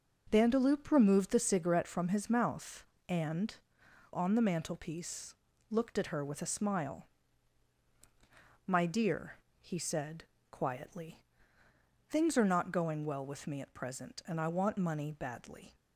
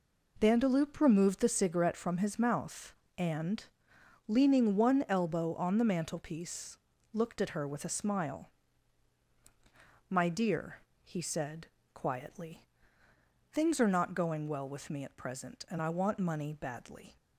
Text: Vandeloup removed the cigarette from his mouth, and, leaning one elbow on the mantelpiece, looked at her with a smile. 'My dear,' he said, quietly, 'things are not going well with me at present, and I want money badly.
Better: second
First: skips "leaning one elbow"; at 3.8 s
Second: none

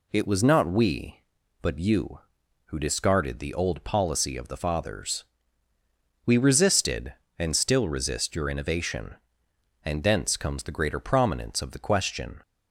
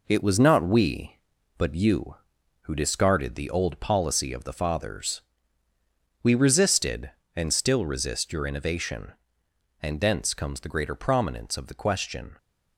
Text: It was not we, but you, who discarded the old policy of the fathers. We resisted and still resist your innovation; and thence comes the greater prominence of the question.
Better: first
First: none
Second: gets quieter; noticeable; throughout; 5.5 dB

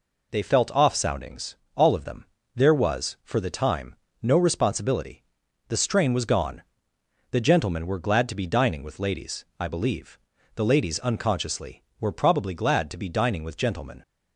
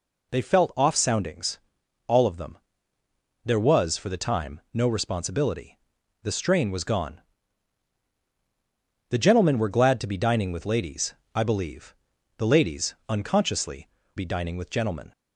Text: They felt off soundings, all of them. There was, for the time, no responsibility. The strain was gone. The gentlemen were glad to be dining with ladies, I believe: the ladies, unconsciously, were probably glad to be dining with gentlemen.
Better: first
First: none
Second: skips "were probably glad to"; at 14.0 s

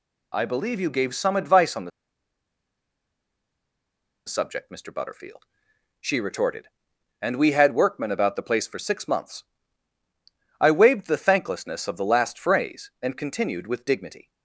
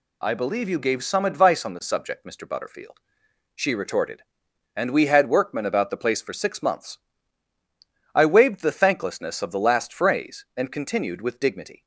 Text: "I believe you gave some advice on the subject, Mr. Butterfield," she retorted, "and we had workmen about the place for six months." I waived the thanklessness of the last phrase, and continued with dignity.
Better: second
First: pauses between "the" and "subject"; strong; at 1.9 s; 2.3 s long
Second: none

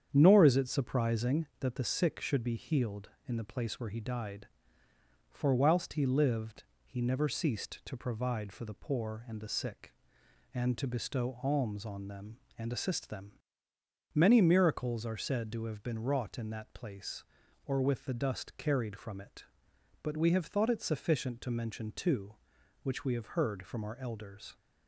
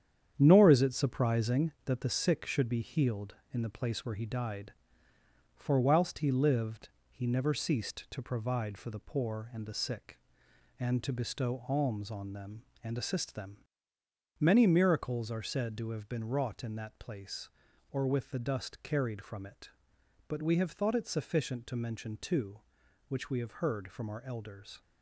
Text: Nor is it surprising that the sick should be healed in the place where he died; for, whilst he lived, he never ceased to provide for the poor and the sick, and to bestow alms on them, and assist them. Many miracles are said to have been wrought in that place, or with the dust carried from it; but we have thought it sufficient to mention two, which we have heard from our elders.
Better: first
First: starts louder than the rest; strong; until 1.1 s; 8.5 dB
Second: gets quieter; noticeable; throughout; 6 dB // starts louder than the rest; strong; until 1.3 s; 9 dB

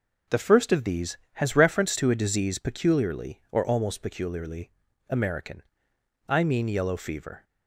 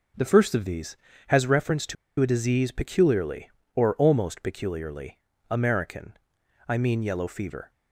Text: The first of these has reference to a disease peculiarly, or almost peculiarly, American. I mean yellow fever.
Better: first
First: none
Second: pauses between "to" and "a"; slight; at 1.9 s; 0.25 s long

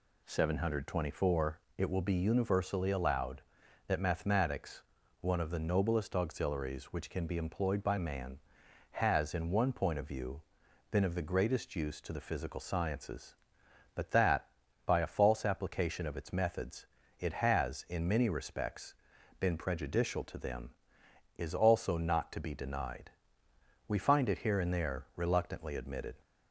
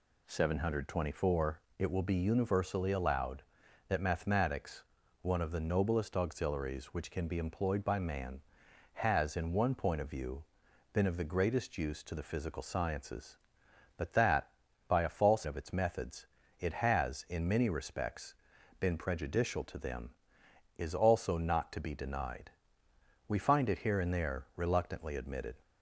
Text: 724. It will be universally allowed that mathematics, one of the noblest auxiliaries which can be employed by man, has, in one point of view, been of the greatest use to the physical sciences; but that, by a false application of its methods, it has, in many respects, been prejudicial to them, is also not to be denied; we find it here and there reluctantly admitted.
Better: first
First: none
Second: skips "application"; at 15.4 s

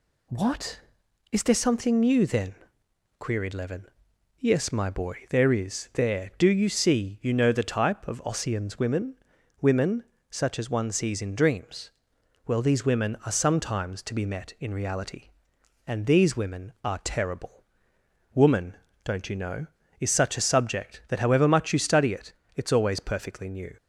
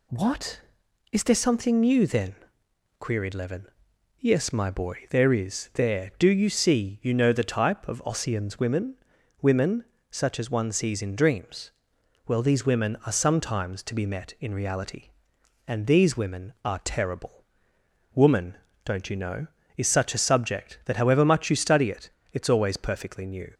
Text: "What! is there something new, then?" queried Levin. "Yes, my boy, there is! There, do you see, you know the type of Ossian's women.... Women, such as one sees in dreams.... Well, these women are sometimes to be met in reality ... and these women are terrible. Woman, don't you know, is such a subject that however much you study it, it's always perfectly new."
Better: neither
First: none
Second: none

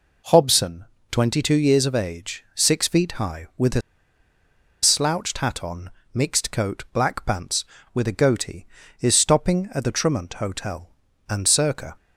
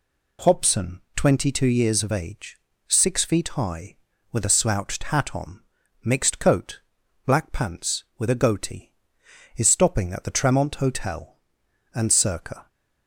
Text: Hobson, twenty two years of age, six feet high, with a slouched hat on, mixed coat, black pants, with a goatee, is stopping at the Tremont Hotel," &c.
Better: second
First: pauses between "a" and "slouched"; at 3.8 s; 1.0 s long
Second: none

